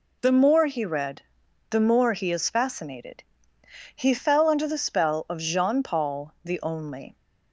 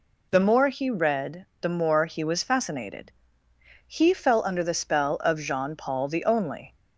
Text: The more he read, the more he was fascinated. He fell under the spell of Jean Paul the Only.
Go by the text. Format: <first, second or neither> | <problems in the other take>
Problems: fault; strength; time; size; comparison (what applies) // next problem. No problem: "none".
second | says "is" for "was"; at 2.3 s